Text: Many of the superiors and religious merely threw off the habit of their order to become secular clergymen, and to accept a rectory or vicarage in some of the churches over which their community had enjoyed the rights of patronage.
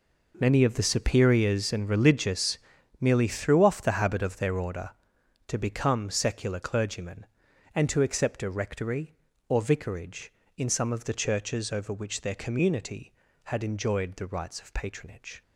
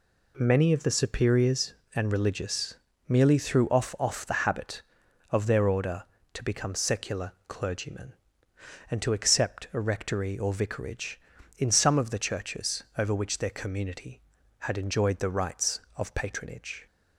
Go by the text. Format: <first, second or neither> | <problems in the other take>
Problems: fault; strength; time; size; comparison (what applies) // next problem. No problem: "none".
first | pauses between "religious" and "merely"; slight; at 2.7 s; 0.34 s long; also in the first // says "off" twice; at 3.9 s // pauses between "secular" and "clergymen"; slight; at 7.3 s; 0.16 s long